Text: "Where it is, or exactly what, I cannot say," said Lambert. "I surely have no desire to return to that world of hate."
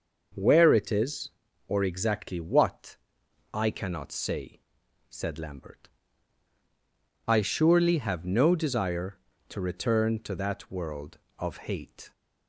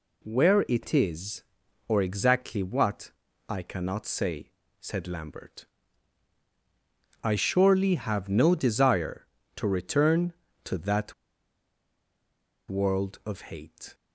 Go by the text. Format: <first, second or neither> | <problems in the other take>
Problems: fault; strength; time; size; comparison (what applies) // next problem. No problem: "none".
first | pauses between "that" and "world"; strong; at 11.1 s; 1.5 s long